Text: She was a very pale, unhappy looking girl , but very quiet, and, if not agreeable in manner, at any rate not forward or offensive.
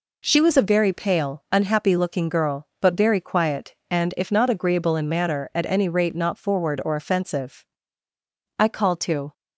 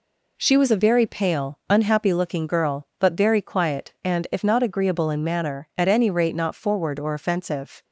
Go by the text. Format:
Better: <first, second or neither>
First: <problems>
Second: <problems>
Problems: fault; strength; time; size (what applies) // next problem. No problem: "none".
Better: second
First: goes on to say "I called to"; noticeable; from 8.5 s on; 0.74 s long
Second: none